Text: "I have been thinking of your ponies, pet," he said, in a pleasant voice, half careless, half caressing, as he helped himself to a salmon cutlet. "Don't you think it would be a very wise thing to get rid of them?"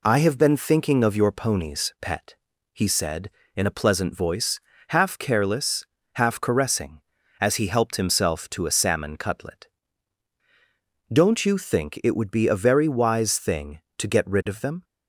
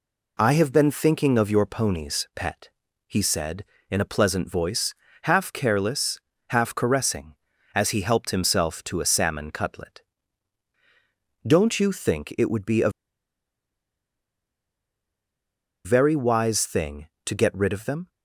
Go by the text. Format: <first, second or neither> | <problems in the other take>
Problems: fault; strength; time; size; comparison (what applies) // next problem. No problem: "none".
first | pauses between "a" and "very"; strong; at 12.8 s; 2.9 s long